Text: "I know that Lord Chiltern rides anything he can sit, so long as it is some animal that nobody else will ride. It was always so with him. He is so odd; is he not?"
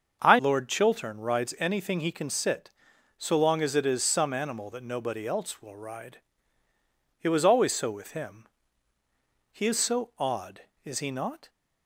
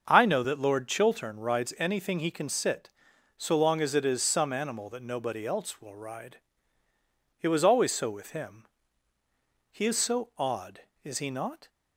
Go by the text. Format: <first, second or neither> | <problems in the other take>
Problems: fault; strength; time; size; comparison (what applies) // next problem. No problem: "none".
second | starts louder than the rest; until 1.2 s; 6.5 dB; also in the second // skips "know that"; at 0.3 s